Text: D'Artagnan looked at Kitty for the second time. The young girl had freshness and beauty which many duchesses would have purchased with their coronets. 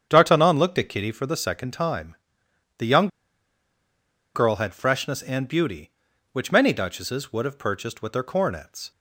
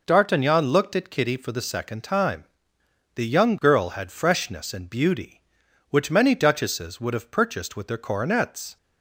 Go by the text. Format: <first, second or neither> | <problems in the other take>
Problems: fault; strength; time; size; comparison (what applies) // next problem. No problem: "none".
second | starts louder than the rest; strong; until 1.1 s; 8.5 dB // pauses between "young" and "girl"; strong; at 3.0 s; 1.2 s long